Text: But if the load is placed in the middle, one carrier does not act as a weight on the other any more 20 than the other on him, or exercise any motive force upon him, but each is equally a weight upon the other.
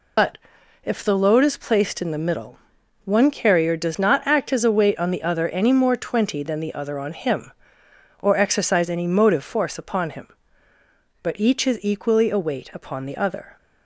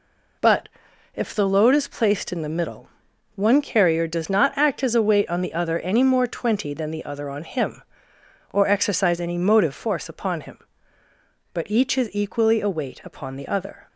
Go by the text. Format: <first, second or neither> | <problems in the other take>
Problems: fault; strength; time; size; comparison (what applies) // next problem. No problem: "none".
second | loses the start of "But"; at 0.1 s; 80 ms // pauses between "But" and "if"; noticeable; at 0.3 s; 0.46 s long; noticeable in the second